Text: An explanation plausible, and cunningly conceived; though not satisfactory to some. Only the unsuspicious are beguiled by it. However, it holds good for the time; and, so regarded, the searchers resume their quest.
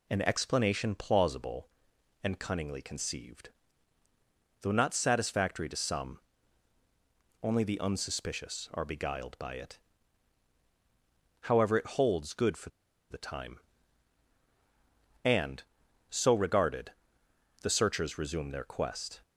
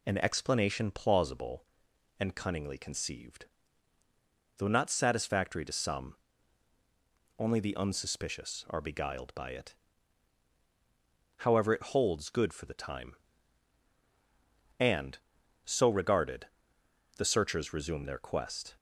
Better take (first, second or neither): second